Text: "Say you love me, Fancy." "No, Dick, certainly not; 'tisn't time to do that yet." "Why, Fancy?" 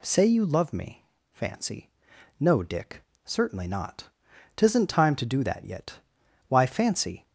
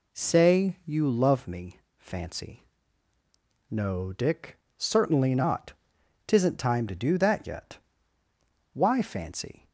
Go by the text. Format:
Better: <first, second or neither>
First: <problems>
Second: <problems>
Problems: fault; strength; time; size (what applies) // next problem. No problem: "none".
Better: neither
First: none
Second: none